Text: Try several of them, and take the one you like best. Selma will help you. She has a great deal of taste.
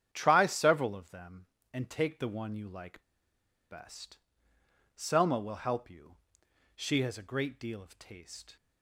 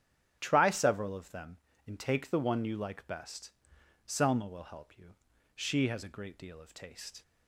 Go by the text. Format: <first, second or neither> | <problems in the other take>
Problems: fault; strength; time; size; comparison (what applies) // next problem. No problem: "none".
second | starts louder than the rest; strong; until 1.1 s; 9 dB; strong in the second // pauses between "like" and "best"; noticeable; at 3.0 s; 0.68 s long